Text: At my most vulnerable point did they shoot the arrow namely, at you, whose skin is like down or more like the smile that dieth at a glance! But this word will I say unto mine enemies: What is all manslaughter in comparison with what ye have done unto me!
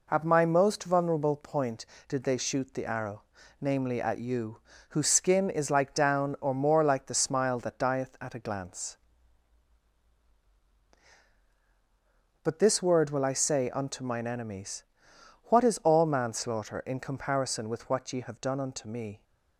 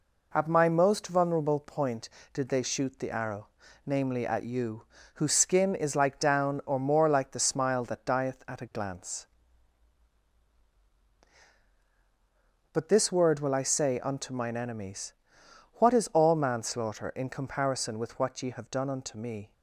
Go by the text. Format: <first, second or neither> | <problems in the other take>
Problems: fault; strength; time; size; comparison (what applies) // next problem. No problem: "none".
neither | pauses between "arrow" and "namely"; slight; the same in both